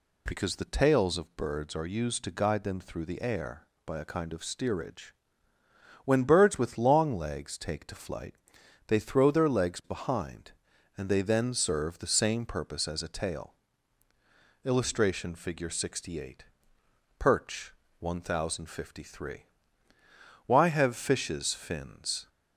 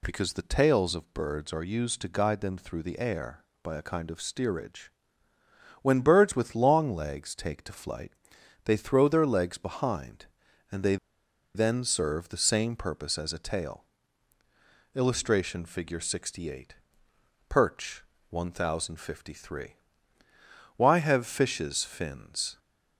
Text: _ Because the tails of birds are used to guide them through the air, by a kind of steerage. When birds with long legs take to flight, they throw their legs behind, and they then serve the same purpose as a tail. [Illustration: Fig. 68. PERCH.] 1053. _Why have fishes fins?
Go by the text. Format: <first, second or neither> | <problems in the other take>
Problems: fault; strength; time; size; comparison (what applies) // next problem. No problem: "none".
first | pauses between "they" and "then"; noticeable; at 10.9 s; 0.58 s long